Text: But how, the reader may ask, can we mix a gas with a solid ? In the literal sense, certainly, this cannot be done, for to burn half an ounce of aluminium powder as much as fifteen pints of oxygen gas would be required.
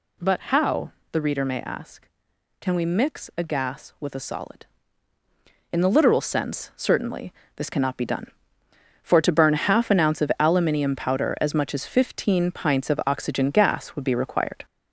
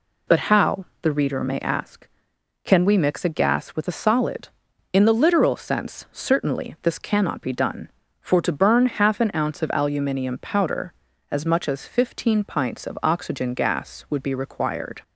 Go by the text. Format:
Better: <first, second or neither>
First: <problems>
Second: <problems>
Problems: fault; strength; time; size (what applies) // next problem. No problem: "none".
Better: second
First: gets louder; throughout; 3.5 dB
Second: none